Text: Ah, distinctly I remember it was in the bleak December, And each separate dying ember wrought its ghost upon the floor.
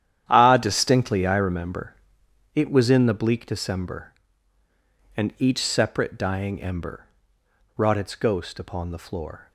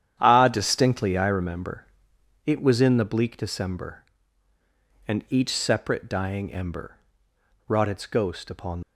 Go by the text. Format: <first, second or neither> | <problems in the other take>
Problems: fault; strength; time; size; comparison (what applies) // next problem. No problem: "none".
first | starts louder than the rest; strong; until 1.2 s; 10 dB; strong in the first // pauses between "remember" and "it"; noticeable; at 1.8 s; 0.60 s long; noticeable in the first // pauses between "ember" and "wrought"; noticeable; at 6.9 s; 0.70 s long; noticeable in the first // stops before "the floor"; at 8.8 s